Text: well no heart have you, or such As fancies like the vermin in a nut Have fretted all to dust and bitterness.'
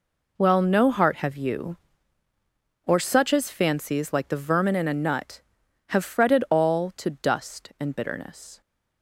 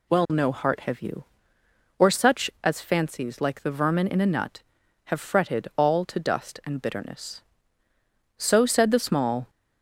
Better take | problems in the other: first | goes on to say "So said the small"; noticeable; from 8.3 s on; 1.1 s long

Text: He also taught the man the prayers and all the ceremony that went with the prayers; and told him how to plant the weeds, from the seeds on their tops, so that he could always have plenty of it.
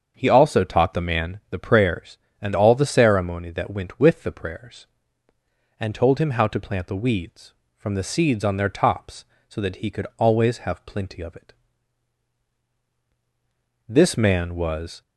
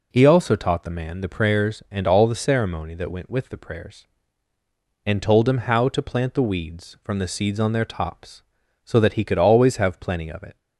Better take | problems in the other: second | starts louder than the rest; until 1.1 s; 7 dB // goes on to say "This man was"; noticeable; from 13.8 s on; 1.1 s long

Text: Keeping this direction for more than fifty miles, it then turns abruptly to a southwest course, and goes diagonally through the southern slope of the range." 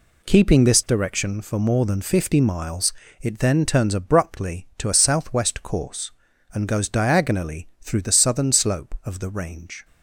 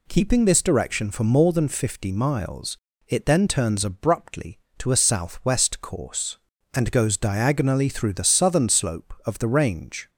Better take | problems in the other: neither | none

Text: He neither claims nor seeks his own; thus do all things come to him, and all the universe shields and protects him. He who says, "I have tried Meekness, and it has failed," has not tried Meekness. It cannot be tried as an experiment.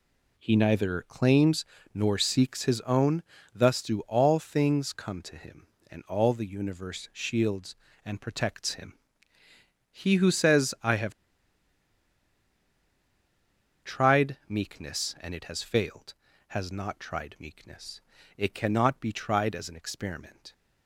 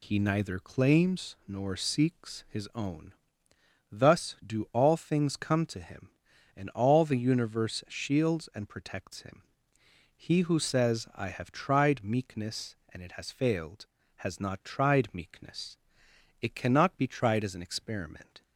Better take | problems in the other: second | pauses between "claims" and "nor"; slight; at 1.6 s; 0.28 s long // pauses between "have" and "tried"; strong; at 11.1 s; 2.7 s long

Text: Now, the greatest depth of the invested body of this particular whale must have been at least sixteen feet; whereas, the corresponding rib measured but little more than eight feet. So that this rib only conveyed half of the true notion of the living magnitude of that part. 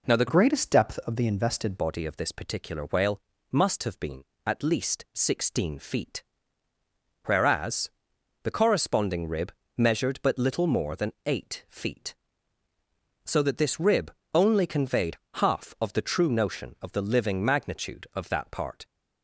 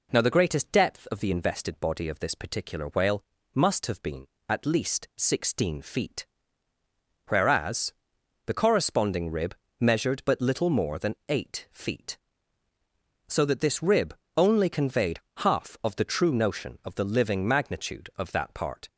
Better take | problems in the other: second | changes voice from "greatest" to "invested"; from 0.2 to 1.7 s; 1.5 s long // pauses between "whale" and "must"; slight; at 3.2 s; 0.30 s long; slight in the second // pauses between "rib" and "measured"; slight; at 9.5 s; 0.28 s long; slight in the second // pauses between "rib" and "only"; slight; at 14.1 s; 0.22 s long; slight in the second // pauses between "conveyed" and "half"; slight; at 15.1 s; 0.18 s long; slight in the second

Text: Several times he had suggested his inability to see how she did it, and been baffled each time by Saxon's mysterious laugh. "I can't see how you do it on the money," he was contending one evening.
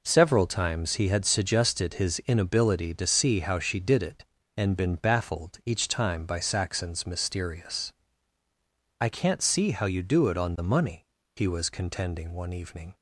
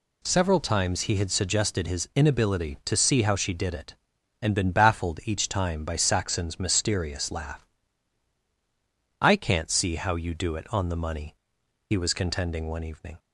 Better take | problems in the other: second | skips "laugh"; at 8.4 s

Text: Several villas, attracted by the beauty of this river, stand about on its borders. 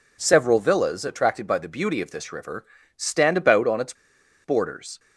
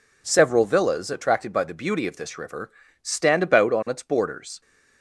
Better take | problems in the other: second | pauses between "its" and "borders"; noticeable; at 3.9 s; 0.51 s long

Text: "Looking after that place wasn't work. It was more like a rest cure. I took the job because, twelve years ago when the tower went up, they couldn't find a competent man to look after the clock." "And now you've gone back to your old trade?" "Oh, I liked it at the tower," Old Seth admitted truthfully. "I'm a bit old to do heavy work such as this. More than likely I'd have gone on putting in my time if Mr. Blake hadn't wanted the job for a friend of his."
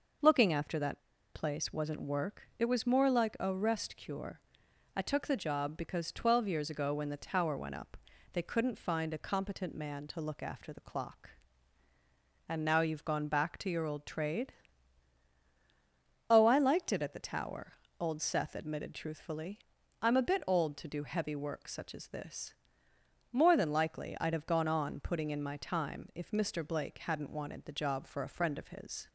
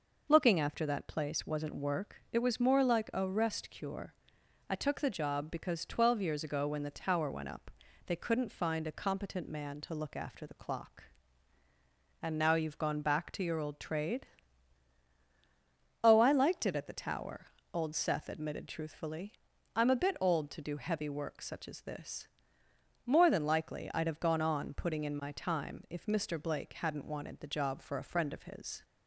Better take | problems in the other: second | pauses between "that" and "place"; slight; at 1.0 s; 0.33 s long

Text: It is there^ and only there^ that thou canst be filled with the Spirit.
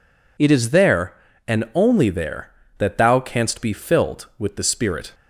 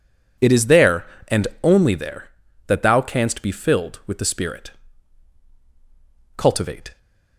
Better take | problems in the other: first | pauses between "and" and "only"; slight; at 1.4 s; 0.16 s long // goes on to say "Cultivate"; noticeable; from 6.3 s on; 0.62 s long

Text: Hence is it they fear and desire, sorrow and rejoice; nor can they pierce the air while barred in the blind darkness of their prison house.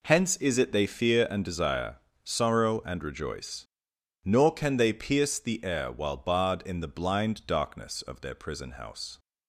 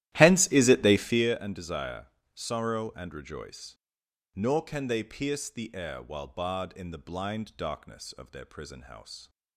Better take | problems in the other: first | starts louder than the rest; strong; until 1.4 s; 14 dB

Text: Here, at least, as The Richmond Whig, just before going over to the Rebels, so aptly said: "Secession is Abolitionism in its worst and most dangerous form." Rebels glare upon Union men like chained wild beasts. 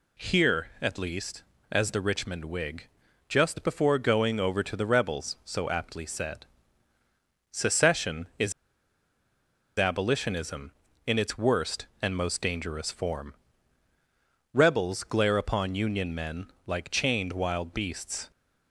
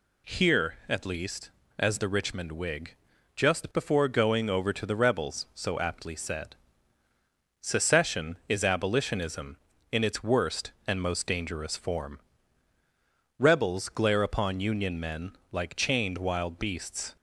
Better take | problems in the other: second | pauses between "is" and "Abolitionism"; strong; at 8.5 s; 1.2 s long // pauses between "men" and "like"; slight; at 16.4 s; 0.18 s long; slight in the second

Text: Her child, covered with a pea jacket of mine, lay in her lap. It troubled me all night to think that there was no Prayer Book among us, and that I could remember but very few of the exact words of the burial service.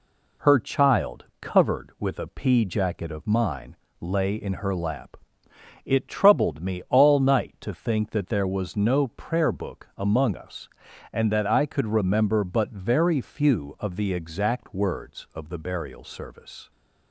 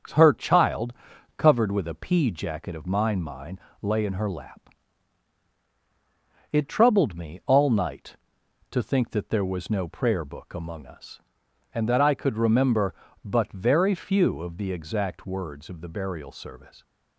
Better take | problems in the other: first | starts louder than the rest; strong; until 1.6 s; 7.5 dB // says "mine" twice; at 3.2 s

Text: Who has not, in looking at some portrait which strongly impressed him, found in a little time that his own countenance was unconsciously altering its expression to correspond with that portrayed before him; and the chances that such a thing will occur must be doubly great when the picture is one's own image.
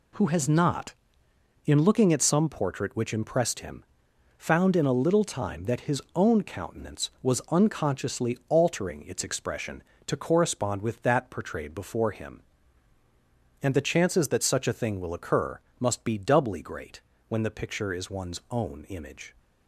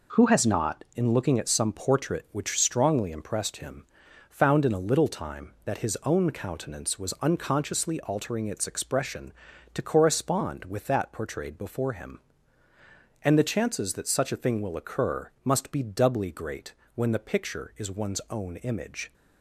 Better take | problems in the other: second | skips "strongly"; at 3.1 s // pauses between "occur" and "must"; slight; at 15.5 s; 0.22 s long // pauses between "great" and "when"; slight; at 16.9 s; 0.28 s long; slight in the second

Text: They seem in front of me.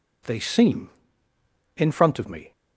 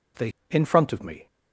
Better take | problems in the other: first | skips "seem"; at 0.3 s

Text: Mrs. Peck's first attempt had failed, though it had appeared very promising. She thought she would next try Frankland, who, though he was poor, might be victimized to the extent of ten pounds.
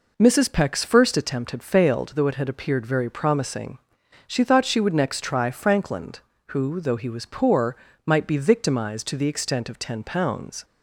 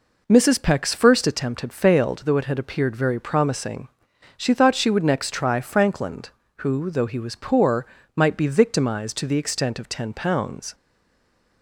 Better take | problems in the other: first | stays silent after the last word; slight; from 10.7 s on; 0.9 s long

